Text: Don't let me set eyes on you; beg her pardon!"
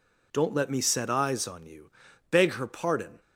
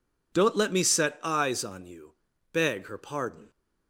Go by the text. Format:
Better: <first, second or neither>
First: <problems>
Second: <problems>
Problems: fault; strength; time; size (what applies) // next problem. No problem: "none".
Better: neither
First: none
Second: none